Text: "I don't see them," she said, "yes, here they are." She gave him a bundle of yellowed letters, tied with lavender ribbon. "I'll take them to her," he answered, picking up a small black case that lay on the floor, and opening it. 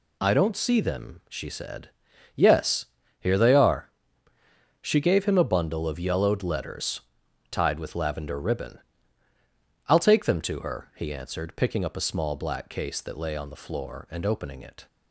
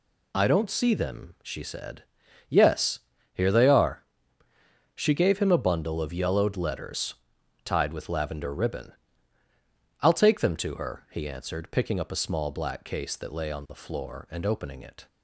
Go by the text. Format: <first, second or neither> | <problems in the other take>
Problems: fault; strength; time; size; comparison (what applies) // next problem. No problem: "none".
neither | none